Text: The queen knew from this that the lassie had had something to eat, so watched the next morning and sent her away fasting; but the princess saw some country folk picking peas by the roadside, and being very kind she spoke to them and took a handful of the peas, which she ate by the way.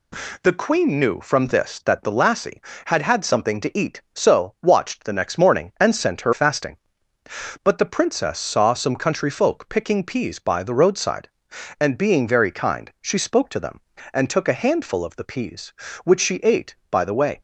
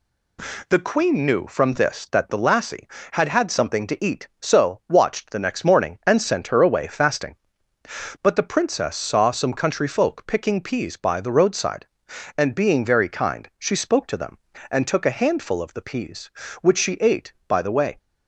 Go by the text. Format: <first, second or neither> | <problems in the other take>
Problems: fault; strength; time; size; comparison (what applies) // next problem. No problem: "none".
second | skips "away"; at 6.3 s